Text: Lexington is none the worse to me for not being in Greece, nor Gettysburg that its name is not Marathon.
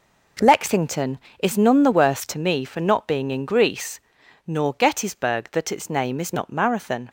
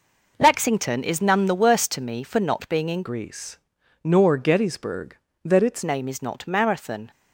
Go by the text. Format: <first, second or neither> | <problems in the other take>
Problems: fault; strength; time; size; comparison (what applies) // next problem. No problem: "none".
first | changes voice from "Greece" to "its"; from 3.0 to 5.8 s; 2.8 s long